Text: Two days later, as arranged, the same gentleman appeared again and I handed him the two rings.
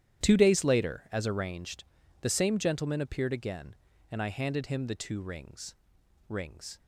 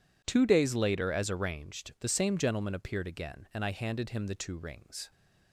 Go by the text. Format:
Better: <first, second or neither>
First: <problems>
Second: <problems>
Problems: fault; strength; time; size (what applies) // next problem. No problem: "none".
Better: second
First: starts louder than the rest; strong; until 1.2 s; 11 dB // says "rings" twice; at 6.2 s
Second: none